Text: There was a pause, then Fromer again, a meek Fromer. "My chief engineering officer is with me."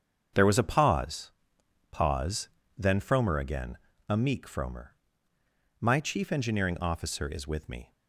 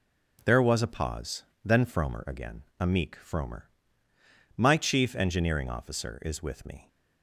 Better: second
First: starts louder than the rest; strong; until 1.9 s; 7 dB // says "pause" twice; at 1.9 s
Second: none

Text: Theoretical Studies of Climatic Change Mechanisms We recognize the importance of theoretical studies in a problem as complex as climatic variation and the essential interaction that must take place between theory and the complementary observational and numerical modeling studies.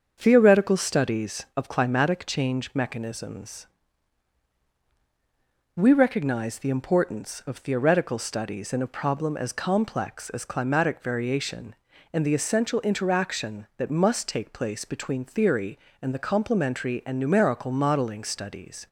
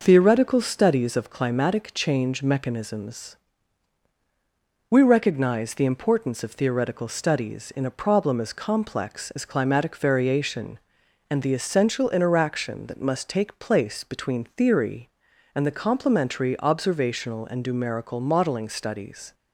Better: second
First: starts louder than the rest; until 1.2 s; 7 dB // pauses between "Mechanisms" and "We"; strong; at 3.6 s; 2.0 s long // skips "observational"; at 17.0 s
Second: pauses between "Mechanisms" and "We"; strong; at 3.3 s; 1.5 s long

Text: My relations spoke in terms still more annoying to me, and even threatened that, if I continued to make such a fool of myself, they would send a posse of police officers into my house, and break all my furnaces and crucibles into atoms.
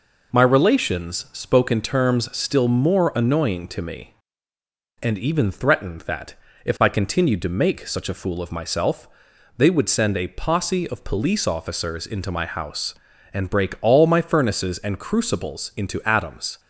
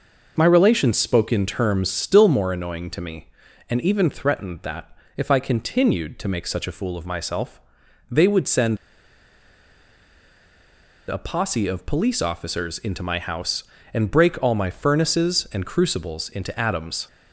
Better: first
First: none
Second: pauses between "send" and "a"; strong; at 8.7 s; 2.3 s long

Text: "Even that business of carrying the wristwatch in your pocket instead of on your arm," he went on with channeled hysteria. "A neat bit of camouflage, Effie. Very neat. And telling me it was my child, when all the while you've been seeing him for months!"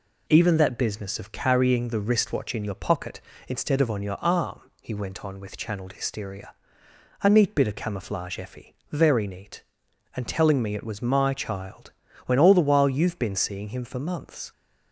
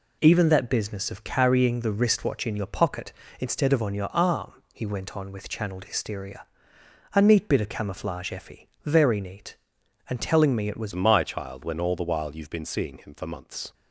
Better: first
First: none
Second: changes voice at "my"; from 10.9 s on; 2.8 s long

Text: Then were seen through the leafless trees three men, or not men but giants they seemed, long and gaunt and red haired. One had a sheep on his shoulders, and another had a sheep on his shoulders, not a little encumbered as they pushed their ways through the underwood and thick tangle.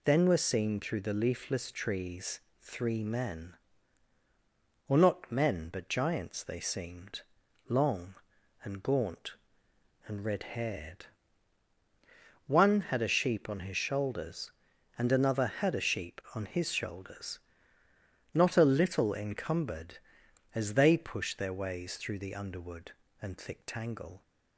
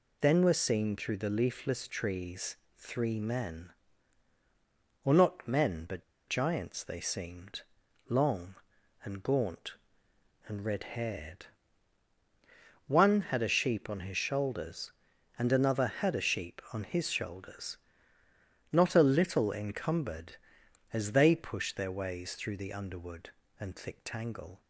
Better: first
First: pauses between "trees" and "three"; slight; at 2.3 s; 0.22 s long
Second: pauses between "trees" and "three"; slight; at 2.5 s; 0.22 s long // pauses between "but" and "giants"; slight; at 6.0 s; 0.26 s long

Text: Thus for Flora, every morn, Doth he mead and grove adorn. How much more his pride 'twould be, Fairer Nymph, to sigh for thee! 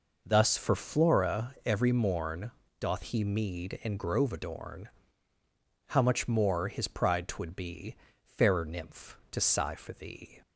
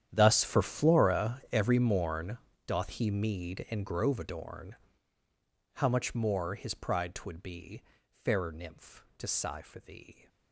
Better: first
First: none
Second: gets quieter; strong; throughout; 18.5 dB

